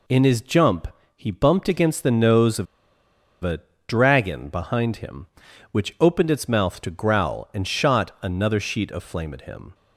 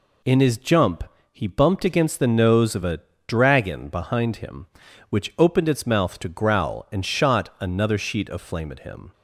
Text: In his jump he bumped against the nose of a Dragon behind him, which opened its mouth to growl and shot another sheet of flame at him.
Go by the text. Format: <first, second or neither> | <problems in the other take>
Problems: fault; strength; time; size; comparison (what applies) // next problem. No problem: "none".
second | pauses between "jump" and "he"; slight; at 0.8 s; 0.30 s long; slight in the second // pauses between "of" and "a"; noticeable; at 2.6 s; 0.78 s long // pauses between "a" and "Dragon"; slight; at 3.6 s; 0.28 s long; slight in the second